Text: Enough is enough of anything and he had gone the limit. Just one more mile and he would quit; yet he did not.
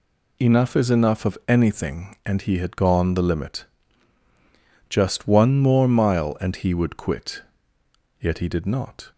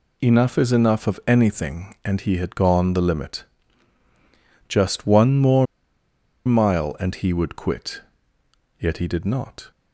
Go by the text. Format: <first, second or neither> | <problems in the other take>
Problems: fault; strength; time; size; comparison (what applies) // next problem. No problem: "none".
first | pauses between "more" and "mile"; noticeable; at 5.6 s; 0.80 s long